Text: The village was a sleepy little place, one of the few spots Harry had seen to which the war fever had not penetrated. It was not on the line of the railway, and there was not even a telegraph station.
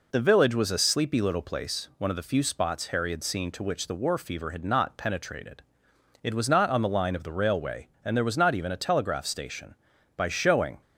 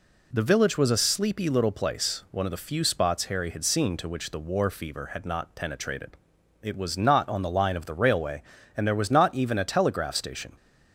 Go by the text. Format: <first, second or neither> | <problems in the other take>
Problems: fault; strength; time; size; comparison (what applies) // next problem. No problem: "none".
second | goes on to say "By showing"; noticeable; from 10.1 s on; 0.64 s long